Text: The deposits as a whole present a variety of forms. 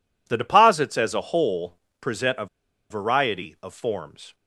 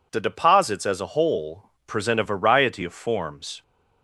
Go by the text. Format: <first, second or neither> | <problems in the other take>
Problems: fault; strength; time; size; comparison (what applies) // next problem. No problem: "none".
second | pauses between "whole" and "present"; slight; at 1.7 s; 0.24 s long; slight in the second // pauses between "a" and "variety"; at 2.4 s; 0.43 s long